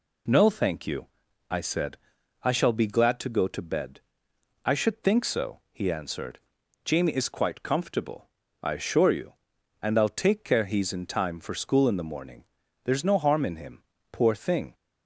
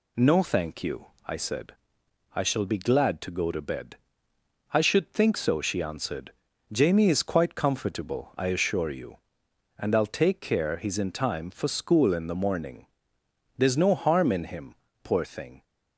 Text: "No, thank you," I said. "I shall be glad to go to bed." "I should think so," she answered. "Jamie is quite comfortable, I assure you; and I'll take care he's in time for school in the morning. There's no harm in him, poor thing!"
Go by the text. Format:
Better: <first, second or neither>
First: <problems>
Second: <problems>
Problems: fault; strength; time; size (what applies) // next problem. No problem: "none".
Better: second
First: says "he" for "she"; at 5.7 s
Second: none